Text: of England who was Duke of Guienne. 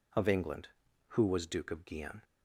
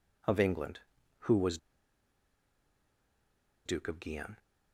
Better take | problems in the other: first | pauses between "was" and "Duke"; strong; at 1.5 s; 2.0 s long

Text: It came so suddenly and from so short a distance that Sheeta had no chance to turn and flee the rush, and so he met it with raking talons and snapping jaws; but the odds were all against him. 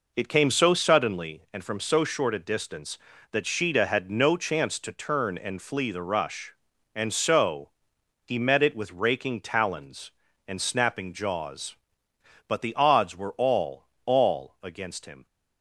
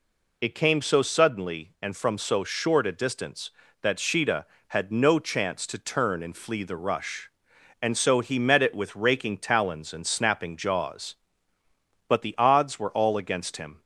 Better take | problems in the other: second | pauses between "so" and "he"; noticeable; at 7.6 s; 0.56 s long // says "all" twice; at 14.0 s

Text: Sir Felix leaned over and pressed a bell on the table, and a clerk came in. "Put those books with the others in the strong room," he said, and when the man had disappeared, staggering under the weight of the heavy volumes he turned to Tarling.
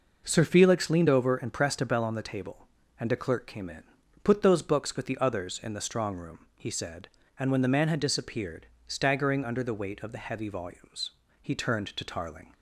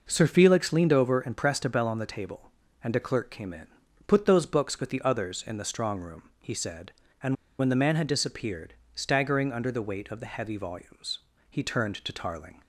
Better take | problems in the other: first | pauses between "and" and "when"; slight; at 7.3 s; 0.23 s long // pauses between "volumes" and "he"; slight; at 11.1 s; 0.30 s long; slight in the first

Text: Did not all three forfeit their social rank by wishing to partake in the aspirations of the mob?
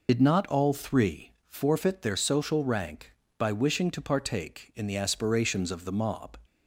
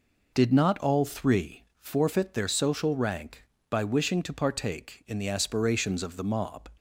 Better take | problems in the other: second | loses the start of "Did"; at 0.0 s; 60 ms // pauses between "three" and "forfeit"; slight; at 1.3 s; 0.16 s long; slight in the second

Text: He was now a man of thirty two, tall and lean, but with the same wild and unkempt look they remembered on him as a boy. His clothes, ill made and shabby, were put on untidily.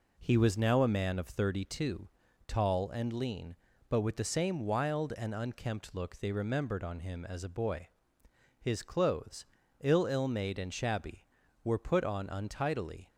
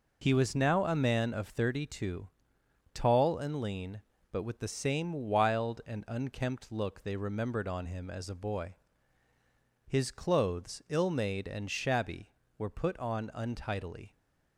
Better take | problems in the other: second | says "ill" twice; at 10.0 s

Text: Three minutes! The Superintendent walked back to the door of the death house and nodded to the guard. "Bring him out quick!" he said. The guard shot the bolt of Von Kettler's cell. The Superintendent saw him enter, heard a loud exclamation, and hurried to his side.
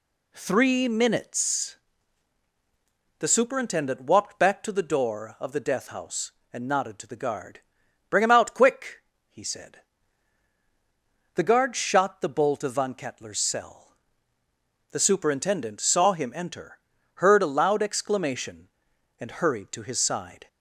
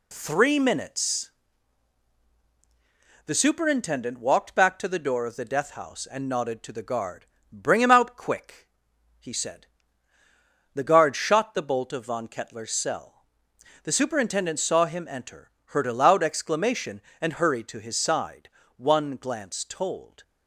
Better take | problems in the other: first | goes on to say "One glance told"; from 18.7 s on; 1.4 s long

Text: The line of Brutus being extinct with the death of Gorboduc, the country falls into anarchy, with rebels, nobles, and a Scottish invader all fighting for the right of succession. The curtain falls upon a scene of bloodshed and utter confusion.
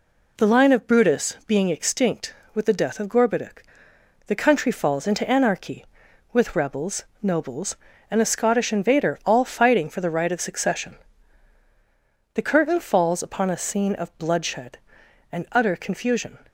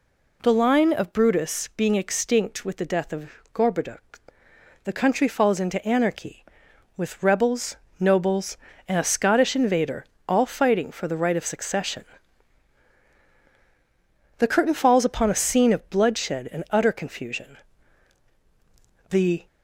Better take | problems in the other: first | pauses between "of" and "Gorboduc"; slight; at 3.2 s; 0.24 s long // pauses between "invader" and "all"; slight; at 10.0 s; 0.24 s long // goes on to say "The"; slight; from 19.0 s on; 0.34 s long

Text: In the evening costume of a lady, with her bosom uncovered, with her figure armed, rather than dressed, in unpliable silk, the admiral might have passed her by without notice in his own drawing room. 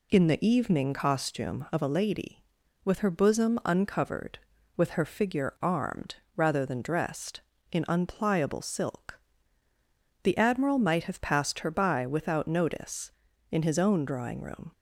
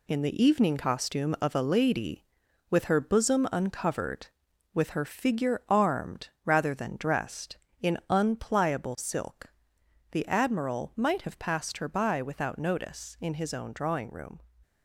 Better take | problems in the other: first | gets quieter; throughout; 6.5 dB

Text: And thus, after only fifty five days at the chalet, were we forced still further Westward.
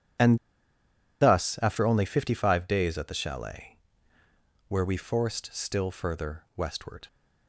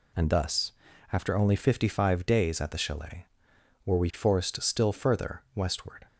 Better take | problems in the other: second | pauses between "And" and "thus"; noticeable; at 0.3 s; 0.83 s long

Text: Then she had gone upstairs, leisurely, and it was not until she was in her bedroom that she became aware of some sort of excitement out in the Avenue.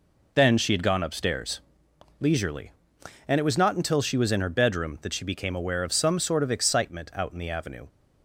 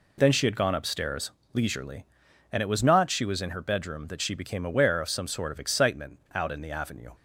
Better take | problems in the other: first | skips "until"; at 3.0 s // pauses between "excitement" and "out"; slight; at 6.1 s; 0.16 s long

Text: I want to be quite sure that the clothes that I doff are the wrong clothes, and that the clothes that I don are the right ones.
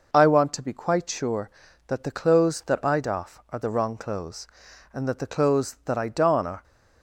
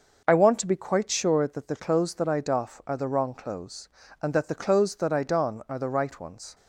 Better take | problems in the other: second | stops before "the right ones"; at 6.6 s

